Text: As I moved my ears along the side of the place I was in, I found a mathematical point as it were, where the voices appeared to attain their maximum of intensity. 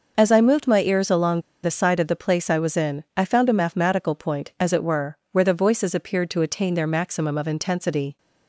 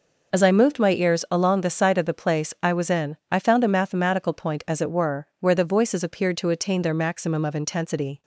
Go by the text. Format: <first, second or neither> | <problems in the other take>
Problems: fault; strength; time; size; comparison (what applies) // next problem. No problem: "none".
second | pauses between "along" and "the"; slight; at 1.3 s; 0.23 s long